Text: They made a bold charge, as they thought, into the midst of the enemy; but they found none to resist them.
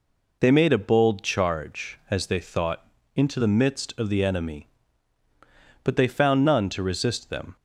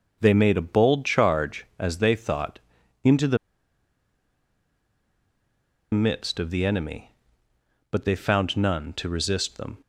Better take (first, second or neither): first